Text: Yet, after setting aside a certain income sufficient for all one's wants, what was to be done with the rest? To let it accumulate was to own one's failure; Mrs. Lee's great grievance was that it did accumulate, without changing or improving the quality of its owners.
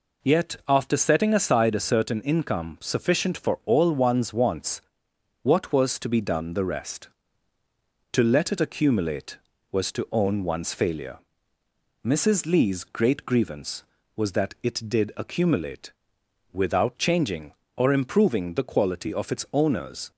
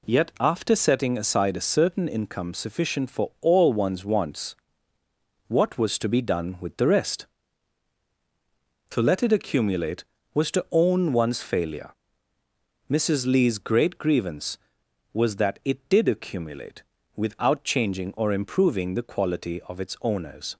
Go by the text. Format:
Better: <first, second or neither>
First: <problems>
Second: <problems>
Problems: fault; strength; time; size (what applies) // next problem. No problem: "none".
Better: second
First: skips "with"; at 6.5 s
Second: none